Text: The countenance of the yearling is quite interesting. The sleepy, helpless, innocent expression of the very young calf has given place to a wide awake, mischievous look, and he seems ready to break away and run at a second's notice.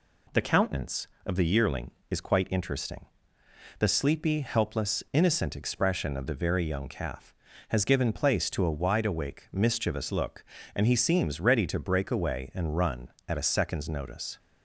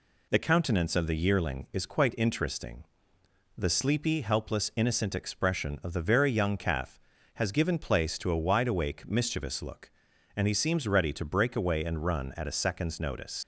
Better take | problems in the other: first | leaves "notice" unfinished; at 13.4 s; 110 ms

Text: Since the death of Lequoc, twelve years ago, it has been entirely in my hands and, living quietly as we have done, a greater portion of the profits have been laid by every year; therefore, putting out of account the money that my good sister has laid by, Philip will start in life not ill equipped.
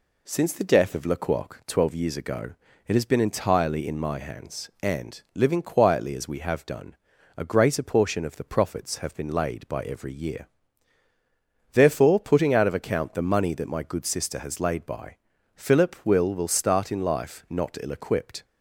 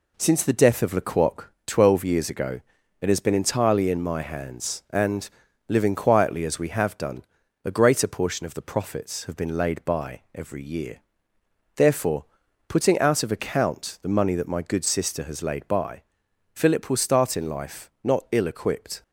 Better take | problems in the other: second | says "will" twice; at 16.3 s

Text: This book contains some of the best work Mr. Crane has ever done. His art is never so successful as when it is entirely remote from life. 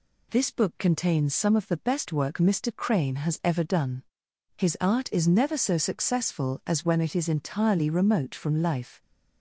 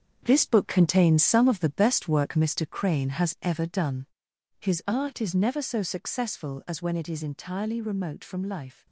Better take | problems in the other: first | gets quieter; strong; throughout; 8.5 dB

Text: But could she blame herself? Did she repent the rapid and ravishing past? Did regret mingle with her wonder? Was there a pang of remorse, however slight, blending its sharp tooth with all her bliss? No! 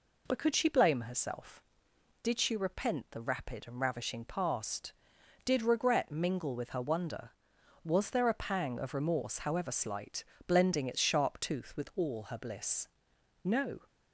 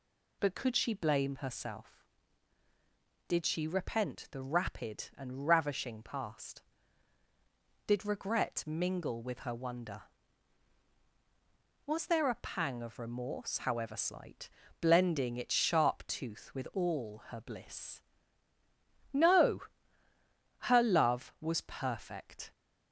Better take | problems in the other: first | goes on to say "Her love was perfect"; strong; from 20.6 s on; 1.9 s long

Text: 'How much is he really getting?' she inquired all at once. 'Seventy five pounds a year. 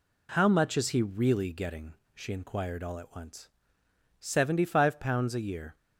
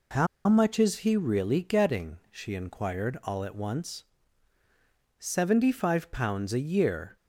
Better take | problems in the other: first | pauses between "How" and "much"; slight; at 0.2 s; 0.21 s long

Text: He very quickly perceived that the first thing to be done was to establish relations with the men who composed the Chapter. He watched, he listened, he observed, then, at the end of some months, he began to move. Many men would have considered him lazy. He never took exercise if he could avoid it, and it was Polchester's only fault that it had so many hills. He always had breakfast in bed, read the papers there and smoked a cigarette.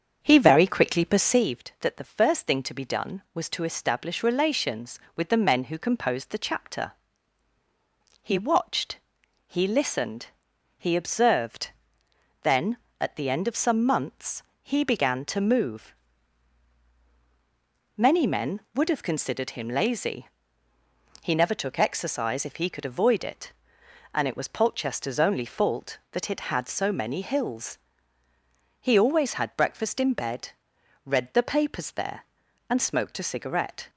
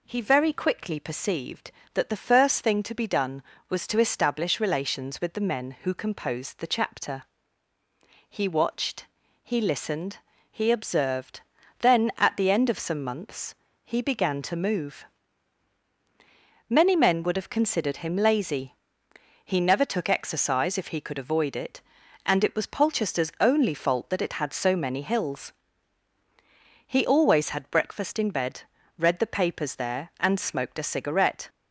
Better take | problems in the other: second | starts louder than the rest; strong; until 1.6 s; 7 dB

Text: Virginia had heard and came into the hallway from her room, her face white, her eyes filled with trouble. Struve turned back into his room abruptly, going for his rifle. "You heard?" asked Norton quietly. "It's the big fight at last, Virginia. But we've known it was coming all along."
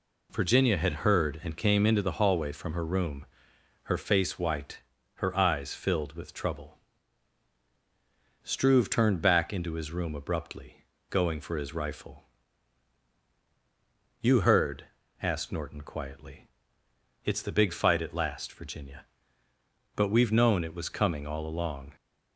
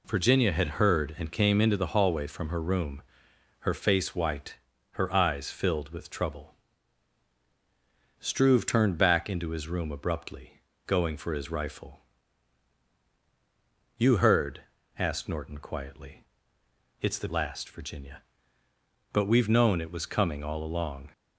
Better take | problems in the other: first | skips "big fight at"; at 17.2 s

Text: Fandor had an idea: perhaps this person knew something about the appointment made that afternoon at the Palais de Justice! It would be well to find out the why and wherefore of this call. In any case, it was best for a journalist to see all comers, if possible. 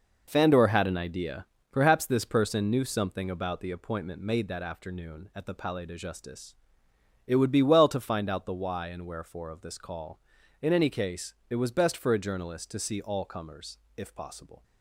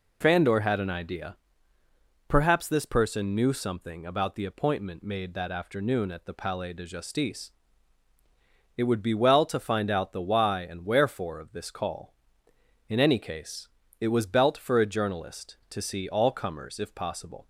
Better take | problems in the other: first | says "belt" for "best"; at 14.2 s

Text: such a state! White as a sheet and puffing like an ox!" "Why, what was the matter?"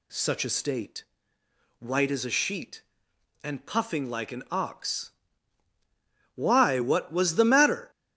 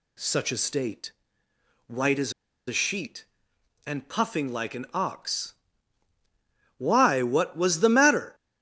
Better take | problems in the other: first | pauses between "as" and "a"; slight; at 2.3 s; 0.35 s long

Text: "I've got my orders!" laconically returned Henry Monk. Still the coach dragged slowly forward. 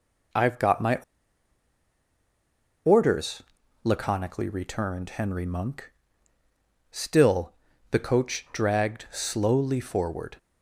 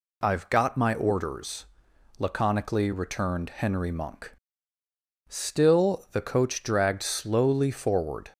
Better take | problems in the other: second | pauses between "my" and "orders"; strong; at 0.9 s; 1.9 s long // pauses between "Still" and "the"; slight; at 7.5 s; 0.34 s long

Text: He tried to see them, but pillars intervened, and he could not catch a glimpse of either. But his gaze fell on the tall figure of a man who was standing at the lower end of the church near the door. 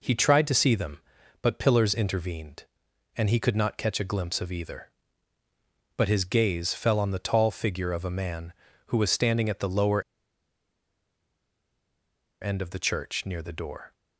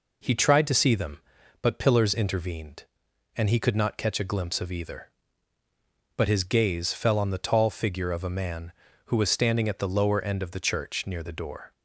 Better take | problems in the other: second | pauses between "lower" and "end"; strong; at 10.0 s; 2.3 s long

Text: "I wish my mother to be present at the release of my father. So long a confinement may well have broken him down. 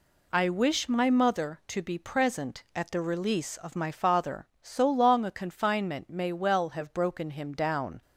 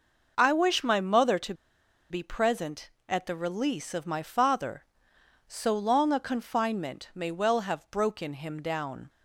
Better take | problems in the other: first | pauses between "to" and "be"; noticeable; at 1.5 s; 0.57 s long

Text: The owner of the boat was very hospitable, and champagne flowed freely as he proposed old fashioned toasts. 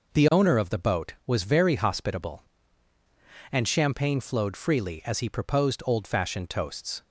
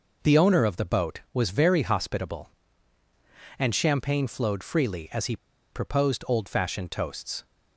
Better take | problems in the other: first | pauses between "he" and "proposed"; at 5.3 s; 0.36 s long

